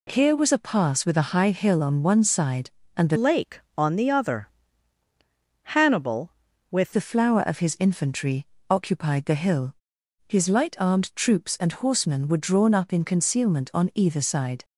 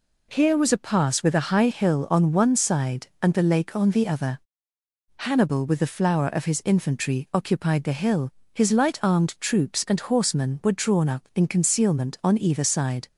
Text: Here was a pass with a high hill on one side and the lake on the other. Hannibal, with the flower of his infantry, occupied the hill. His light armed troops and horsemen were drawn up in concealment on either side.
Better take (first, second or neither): second